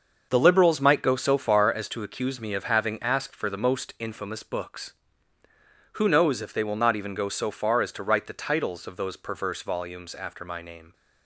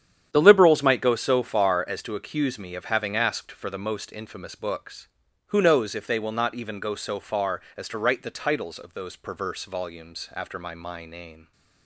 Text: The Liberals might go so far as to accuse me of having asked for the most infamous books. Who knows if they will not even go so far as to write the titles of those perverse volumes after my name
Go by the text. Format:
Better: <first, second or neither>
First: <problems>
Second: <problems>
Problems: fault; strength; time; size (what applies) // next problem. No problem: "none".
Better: first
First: starts louder than the rest; until 1.3 s; 6.5 dB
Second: starts louder than the rest; strong; until 1.3 s; 9.5 dB // says "my" twice; at 10.7 s